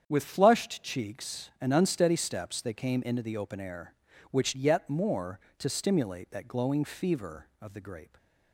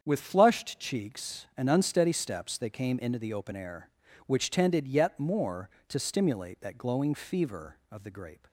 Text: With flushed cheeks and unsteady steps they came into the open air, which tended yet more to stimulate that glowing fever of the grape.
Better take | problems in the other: second | starts louder than the rest; strong; until 1.0 s; 8 dB; strong in the second // skips "tended"; at 4.5 s

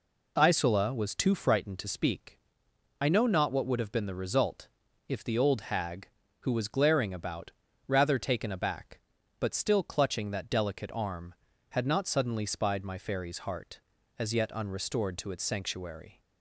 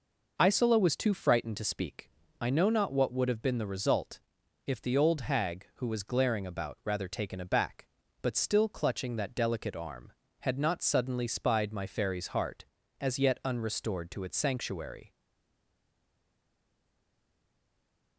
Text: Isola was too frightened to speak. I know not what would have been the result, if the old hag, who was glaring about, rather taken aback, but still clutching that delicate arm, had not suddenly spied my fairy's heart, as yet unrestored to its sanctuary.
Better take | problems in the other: first | stays silent after the last word; strong; from 15.0 s on; 3.1 s long

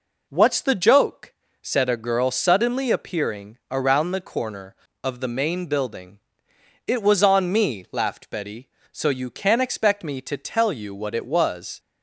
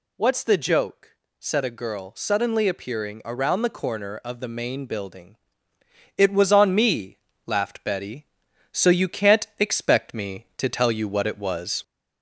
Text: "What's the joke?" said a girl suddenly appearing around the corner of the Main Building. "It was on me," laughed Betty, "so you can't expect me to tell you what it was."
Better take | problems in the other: first | gets louder; slight; throughout; 2 dB

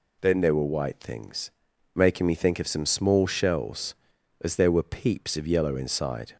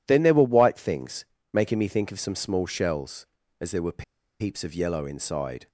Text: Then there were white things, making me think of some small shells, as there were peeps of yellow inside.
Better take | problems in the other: first | pauses between "were" and "peeps"; at 4.0 s; 0.36 s long

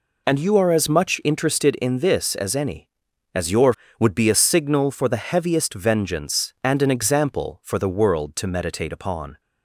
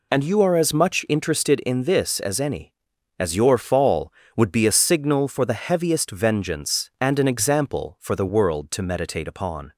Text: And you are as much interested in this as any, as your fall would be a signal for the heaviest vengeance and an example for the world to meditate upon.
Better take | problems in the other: second | skips "fall"; at 3.8 s

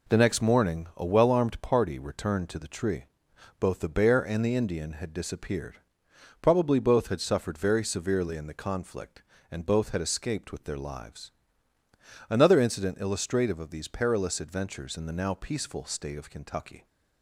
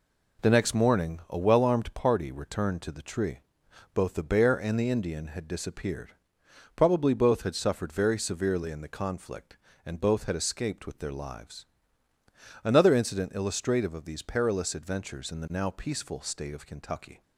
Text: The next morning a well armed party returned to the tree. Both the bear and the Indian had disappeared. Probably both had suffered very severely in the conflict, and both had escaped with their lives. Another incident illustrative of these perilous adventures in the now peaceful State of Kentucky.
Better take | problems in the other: neither | none

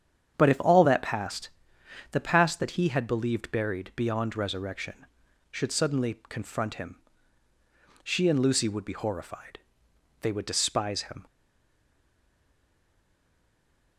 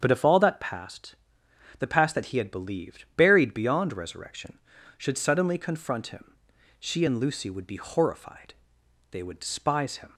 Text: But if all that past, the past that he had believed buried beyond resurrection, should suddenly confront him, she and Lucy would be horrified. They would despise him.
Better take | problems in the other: second | starts louder than the rest; strong; until 1.3 s; 8.5 dB; strong in the second // stays silent after the last word; strong; from 11.2 s on; 2.7 s long

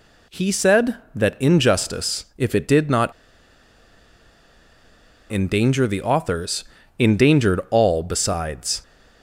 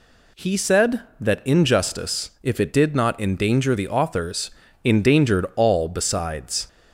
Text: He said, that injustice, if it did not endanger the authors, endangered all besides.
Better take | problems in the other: second | pauses between "not" and "endanger"; strong; at 3.1 s; 2.1 s long

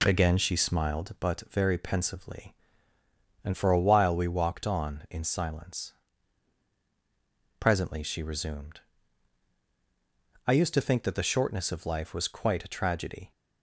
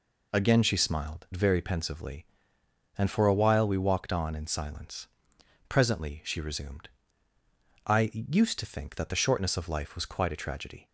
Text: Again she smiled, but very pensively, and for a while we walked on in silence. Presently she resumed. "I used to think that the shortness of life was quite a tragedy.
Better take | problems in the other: first | skips "but"; at 1.3 s

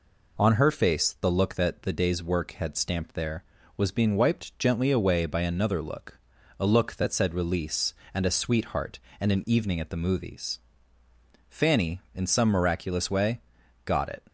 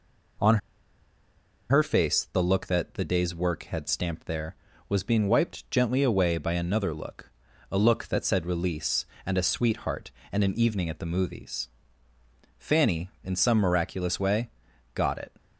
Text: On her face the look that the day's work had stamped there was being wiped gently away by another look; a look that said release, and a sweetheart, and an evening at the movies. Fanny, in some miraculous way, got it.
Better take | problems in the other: first | pauses between "On" and "her"; at 0.5 s; 1.1 s long

